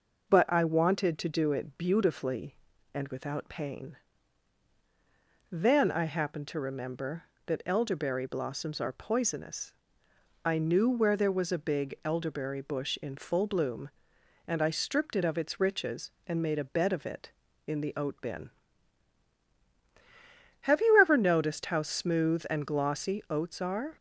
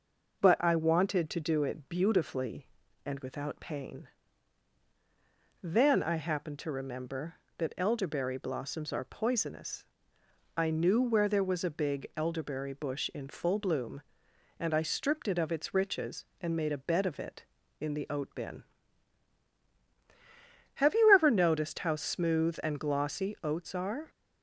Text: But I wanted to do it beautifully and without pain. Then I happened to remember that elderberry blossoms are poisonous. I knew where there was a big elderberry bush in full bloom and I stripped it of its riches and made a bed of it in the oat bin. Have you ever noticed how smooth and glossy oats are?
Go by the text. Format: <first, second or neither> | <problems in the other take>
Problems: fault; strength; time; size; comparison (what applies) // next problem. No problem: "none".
neither | none